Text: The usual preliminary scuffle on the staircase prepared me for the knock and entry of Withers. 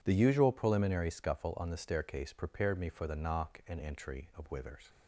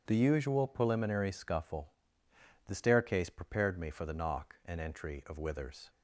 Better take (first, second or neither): first